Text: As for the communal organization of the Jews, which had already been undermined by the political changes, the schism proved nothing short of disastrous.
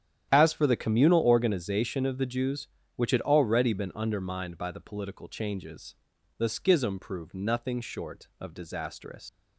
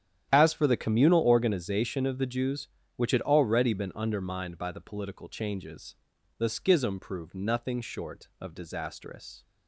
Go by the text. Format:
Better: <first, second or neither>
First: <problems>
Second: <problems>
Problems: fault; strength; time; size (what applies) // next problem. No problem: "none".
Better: second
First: starts louder than the rest; strong; until 1.3 s; 10 dB // leaves "disastrous" unfinished; at 9.2 s; 135 ms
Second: starts louder than the rest; strong; until 1.3 s; 10 dB